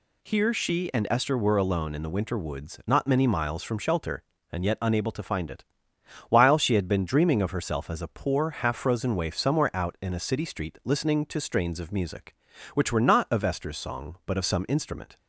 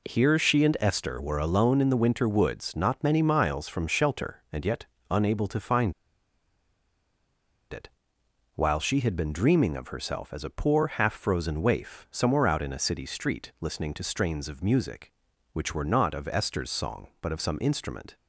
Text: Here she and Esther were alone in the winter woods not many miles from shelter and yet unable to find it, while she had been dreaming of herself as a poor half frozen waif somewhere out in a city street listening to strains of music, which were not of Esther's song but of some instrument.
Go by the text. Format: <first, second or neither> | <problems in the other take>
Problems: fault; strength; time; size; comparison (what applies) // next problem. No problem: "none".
first | pauses between "yet" and "unable"; slight; at 4.8 s; 0.24 s long // pauses between "find" and "it"; strong; at 5.9 s; 1.7 s long